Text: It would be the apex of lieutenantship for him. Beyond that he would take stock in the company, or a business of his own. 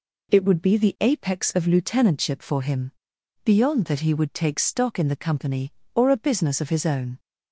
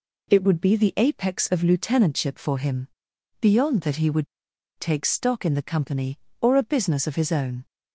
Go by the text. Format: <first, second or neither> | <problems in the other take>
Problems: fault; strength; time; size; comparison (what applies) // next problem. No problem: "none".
first | pauses between "would" and "take"; noticeable; at 4.2 s; 0.52 s long